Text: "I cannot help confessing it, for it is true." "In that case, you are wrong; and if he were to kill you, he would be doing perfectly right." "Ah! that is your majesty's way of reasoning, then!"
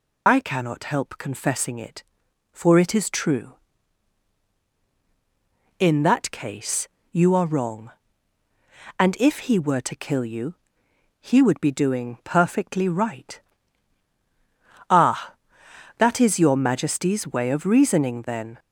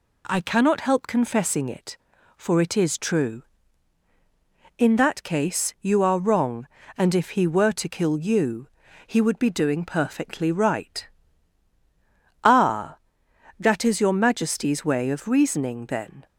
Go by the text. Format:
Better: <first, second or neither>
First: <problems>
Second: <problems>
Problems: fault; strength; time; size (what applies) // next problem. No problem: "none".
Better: second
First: loses the start of "I"; at 0.2 s; 55 ms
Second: none